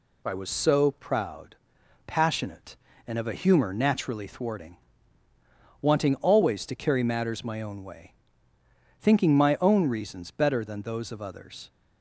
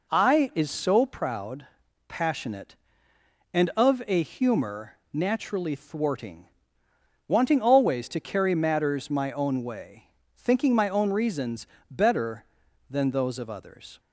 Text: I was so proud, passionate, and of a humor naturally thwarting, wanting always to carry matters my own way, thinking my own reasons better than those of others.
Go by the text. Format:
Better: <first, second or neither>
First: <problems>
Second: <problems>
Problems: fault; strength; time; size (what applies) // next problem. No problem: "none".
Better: first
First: none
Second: says "is" for "was"; at 0.5 s // pauses between "humor" and "naturally"; slight; at 4.9 s; 0.16 s long // pauses between "reasons" and "better"; slight; at 11.6 s; 0.24 s long